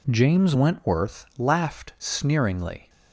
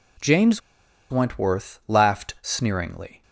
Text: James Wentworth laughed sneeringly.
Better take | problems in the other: first | pauses between "James" and "Wentworth"; noticeable; at 0.6 s; 0.50 s long

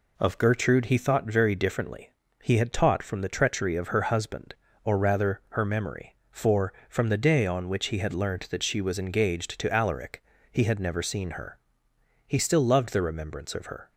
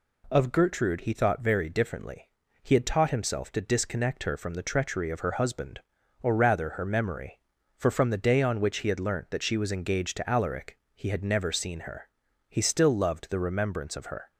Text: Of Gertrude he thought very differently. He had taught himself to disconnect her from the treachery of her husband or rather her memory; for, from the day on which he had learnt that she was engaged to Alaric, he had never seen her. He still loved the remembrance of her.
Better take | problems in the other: second | skips "himself to disconnect her"; at 3.0 s

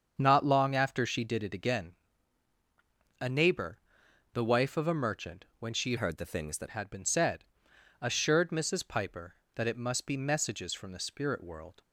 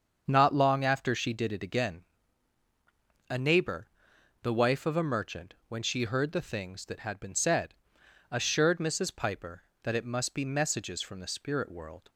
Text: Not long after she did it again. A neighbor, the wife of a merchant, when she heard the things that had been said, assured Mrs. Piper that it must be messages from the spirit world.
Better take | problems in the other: second | starts louder than the rest; until 1.1 s; 7 dB; also in the second // changes voice from "heard" to "that"; from 5.9 to 6.6 s; 0.7 s long

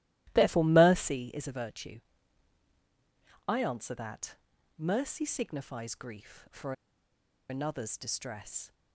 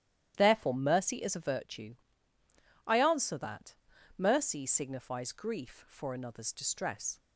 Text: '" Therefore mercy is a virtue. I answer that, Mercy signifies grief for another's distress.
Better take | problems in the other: second | starts louder than the rest; strong; until 1.3 s; 15.5 dB; strong in the second // pauses between "for" and "another's"; noticeable; at 6.7 s; 0.77 s long

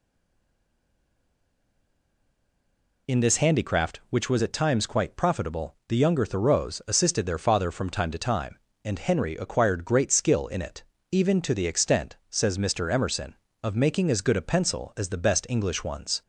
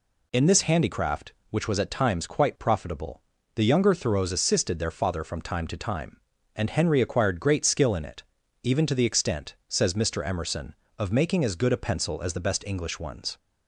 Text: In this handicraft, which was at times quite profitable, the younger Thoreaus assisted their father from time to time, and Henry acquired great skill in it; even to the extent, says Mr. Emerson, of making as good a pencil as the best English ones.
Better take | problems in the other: second | stays silent before the first word; strong; until 3.0 s; 3.0 s long

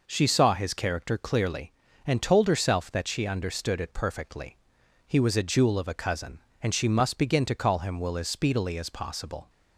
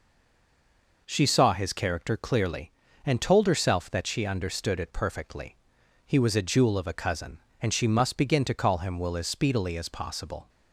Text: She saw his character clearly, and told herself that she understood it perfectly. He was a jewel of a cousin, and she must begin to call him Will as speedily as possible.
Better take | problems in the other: first | stays silent before the first word; until 1.0 s; 1.0 s long

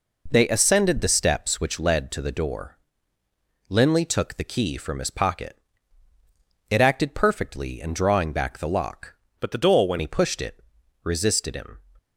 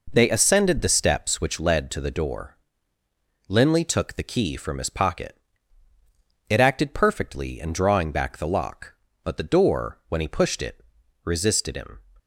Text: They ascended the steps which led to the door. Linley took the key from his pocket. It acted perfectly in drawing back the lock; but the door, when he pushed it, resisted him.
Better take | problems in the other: second | changes voice from "but" to "when"; from 9.3 to 9.9 s; 0.6 s long

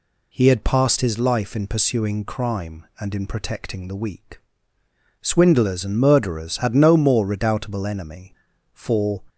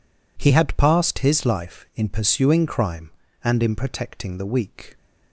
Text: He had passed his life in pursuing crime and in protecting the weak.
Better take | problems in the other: second | goes on to say "Swindlers and murderers had no more redoubtable enemy for"; strong; from 5.2 s on; 4.0 s long

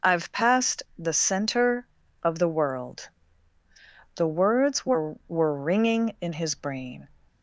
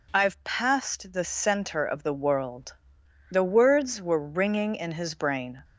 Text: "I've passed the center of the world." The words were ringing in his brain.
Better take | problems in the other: second | pauses between "passed" and "the"; slight; at 0.8 s; 0.16 s long // says "were" twice; at 5.2 s

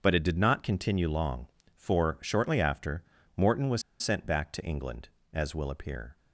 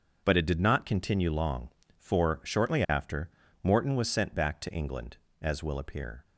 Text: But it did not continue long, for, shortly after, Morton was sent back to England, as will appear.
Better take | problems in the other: second | starts louder than the rest; until 1.0 s; 6.5 dB; also in the second // pauses between "was" and "sent"; slight; at 3.8 s; 0.18 s long

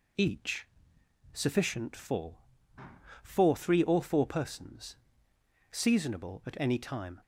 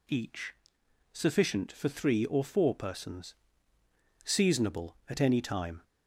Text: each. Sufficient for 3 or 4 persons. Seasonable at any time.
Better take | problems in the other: second | says "for" twice; at 3.2 s

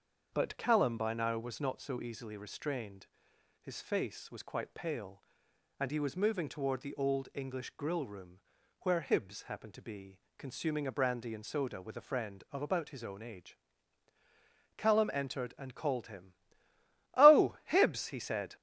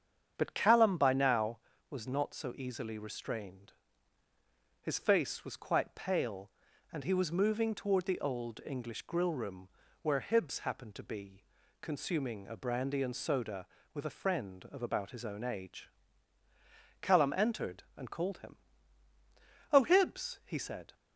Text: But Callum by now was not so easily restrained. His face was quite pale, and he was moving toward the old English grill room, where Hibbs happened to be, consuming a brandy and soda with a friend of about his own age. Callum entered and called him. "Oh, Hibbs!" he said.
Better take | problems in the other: neither | starts louder than the rest; the same in both

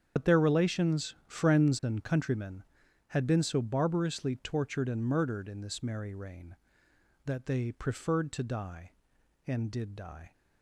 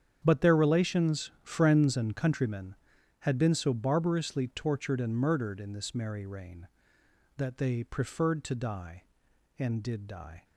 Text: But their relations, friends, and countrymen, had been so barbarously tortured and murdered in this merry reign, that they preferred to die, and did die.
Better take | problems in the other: second | loses the start of "But"; at 0.1 s; 90 ms // starts louder than the rest; strong; until 1.2 s; 7.5 dB; strong in the second

